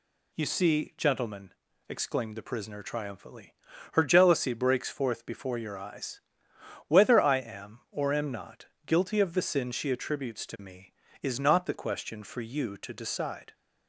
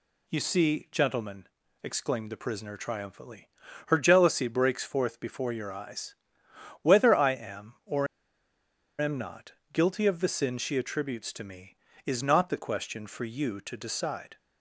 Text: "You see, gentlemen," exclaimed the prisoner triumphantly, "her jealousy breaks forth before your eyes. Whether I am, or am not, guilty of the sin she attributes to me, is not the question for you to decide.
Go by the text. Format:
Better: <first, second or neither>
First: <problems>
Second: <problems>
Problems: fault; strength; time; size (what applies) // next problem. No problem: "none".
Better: first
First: none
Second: pauses between "or" and "am"; noticeable; at 8.0 s; 0.94 s long